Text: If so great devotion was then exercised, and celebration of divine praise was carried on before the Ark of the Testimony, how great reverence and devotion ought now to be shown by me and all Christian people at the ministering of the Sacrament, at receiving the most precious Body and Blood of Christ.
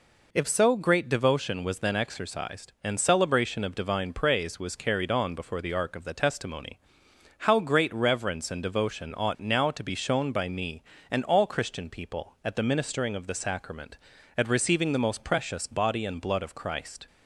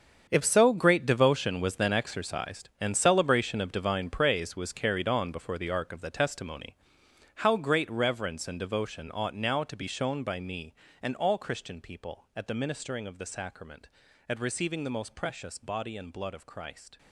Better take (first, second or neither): first